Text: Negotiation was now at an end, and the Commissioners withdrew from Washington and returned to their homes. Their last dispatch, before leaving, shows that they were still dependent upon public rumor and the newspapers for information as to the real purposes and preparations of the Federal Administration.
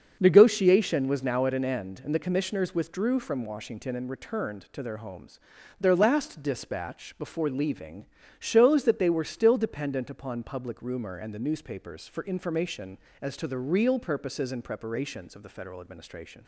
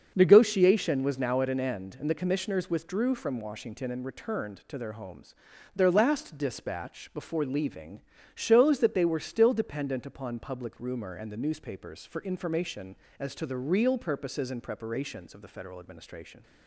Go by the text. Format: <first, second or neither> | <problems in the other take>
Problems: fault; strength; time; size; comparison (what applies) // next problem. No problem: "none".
neither | starts louder than the rest; the same in both